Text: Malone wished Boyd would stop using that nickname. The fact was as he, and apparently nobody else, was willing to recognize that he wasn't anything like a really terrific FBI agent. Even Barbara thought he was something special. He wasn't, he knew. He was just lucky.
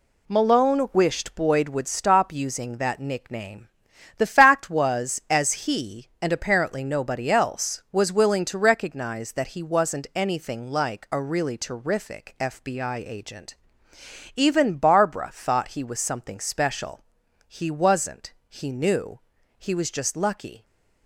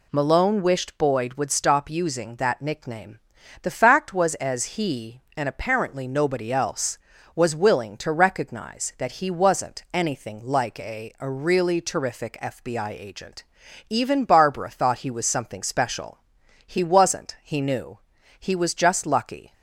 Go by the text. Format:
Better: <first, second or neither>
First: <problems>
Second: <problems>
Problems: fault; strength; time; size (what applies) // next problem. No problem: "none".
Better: first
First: none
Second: says "a" twice; at 11.2 s